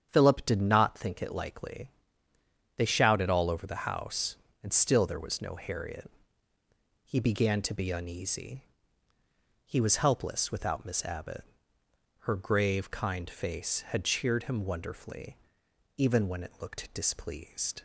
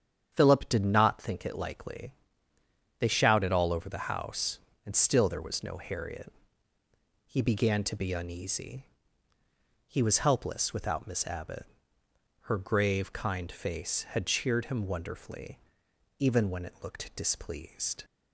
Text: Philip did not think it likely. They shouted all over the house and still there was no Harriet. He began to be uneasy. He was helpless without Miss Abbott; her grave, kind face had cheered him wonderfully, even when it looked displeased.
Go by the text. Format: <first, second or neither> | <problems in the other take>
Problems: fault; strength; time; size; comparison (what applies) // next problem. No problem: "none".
neither | starts louder than the rest; strong; the same in both